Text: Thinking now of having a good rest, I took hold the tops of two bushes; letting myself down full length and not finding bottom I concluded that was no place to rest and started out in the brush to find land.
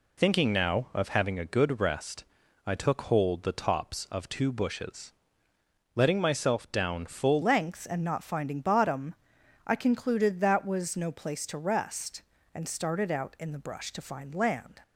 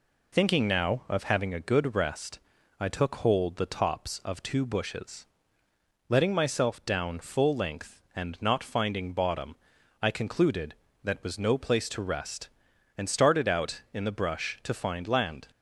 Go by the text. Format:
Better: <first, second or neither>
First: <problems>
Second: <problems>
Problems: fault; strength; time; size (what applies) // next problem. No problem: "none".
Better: second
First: changes voice at "length"; from 7.4 s on; 7.4 s long // pauses between "bottom" and "I"; noticeable; at 9.1 s; 0.54 s long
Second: pauses between "bottom" and "I"; at 9.5 s; 0.44 s long